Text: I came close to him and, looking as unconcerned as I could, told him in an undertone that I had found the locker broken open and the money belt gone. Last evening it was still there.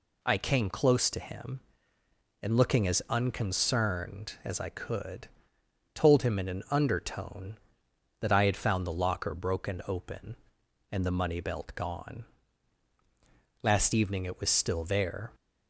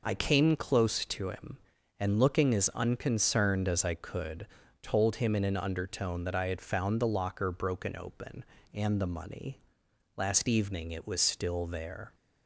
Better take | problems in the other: first | skips "belt gone"; at 9.8 s

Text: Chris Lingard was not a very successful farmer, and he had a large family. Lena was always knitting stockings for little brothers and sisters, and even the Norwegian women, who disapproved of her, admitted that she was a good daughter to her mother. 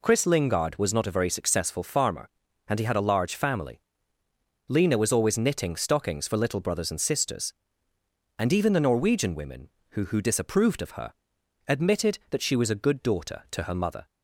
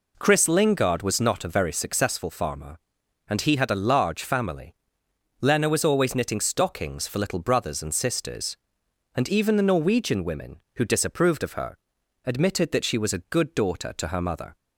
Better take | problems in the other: second | says "who" twice; at 10.0 s

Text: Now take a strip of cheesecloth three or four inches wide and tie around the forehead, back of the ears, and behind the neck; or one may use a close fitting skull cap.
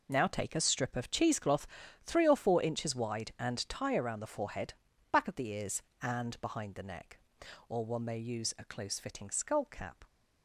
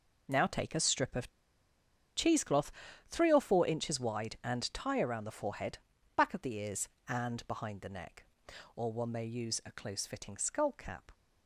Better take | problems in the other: first | pauses between "of" and "cheesecloth"; noticeable; at 1.2 s; 0.87 s long // pauses between "cheesecloth" and "three"; at 2.6 s; 0.38 s long; also in the first

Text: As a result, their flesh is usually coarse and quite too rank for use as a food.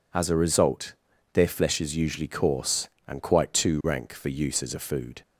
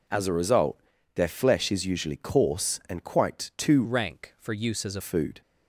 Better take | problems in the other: first | changes voice from "rank" to "a"; from 3.8 to 5.0 s; 1.2 s long

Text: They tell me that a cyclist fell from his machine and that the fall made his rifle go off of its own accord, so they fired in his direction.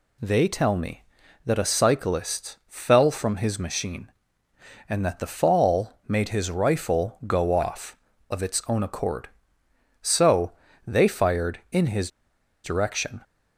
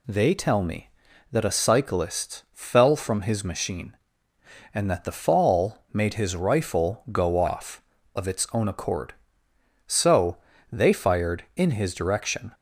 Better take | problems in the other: second | pauses between "so" and "they"; slight; at 10.5 s; 0.34 s long; slight in the second // pauses between "his" and "direction"; noticeable; at 12.0 s; 0.54 s long

